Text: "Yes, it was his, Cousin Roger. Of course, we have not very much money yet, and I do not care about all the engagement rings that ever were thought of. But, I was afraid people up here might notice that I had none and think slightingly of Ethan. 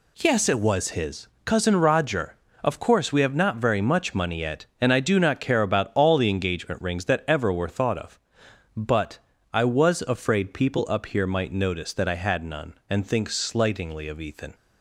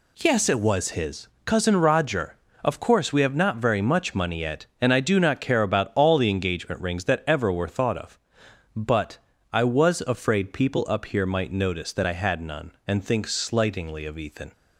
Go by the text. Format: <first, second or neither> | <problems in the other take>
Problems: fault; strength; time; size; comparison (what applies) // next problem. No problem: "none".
neither | none